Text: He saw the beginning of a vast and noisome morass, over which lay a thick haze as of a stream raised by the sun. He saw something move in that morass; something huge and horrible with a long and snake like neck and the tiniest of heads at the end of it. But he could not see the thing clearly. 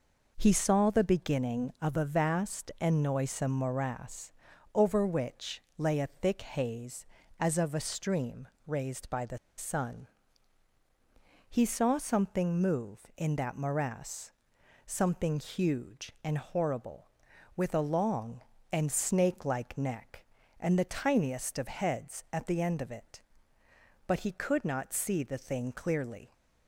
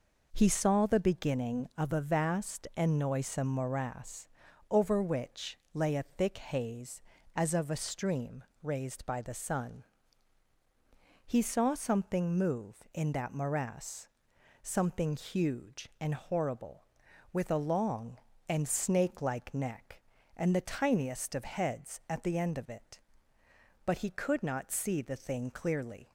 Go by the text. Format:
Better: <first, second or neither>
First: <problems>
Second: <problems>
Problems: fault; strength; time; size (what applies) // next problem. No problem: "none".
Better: second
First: pauses between "which" and "lay"; slight; at 5.6 s; 0.16 s long // pauses between "stream" and "raised"; slight; at 8.4 s; 0.20 s long // pauses between "the" and "sun"; slight; at 9.3 s; 0.20 s long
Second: pauses between "which" and "lay"; slight; at 5.5 s; 0.16 s long // pauses between "stream" and "raised"; slight; at 8.4 s; 0.20 s long